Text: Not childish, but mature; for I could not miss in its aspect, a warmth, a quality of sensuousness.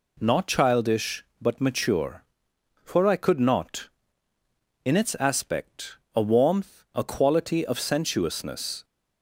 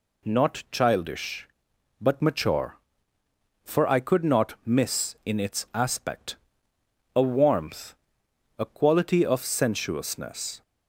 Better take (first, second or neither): second